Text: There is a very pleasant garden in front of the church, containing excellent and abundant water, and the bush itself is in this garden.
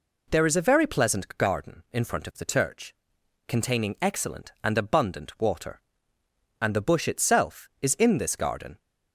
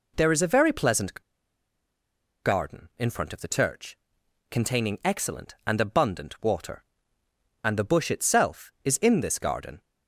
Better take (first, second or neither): first